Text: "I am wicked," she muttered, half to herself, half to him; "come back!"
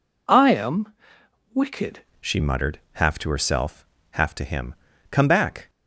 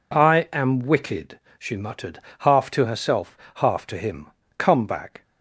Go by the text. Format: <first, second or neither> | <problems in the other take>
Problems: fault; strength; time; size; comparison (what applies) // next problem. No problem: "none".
second | pauses between "am" and "wicked"; noticeable; at 0.9 s; 0.62 s long // changes voice at "she"; from 2.1 s on; 3.5 s long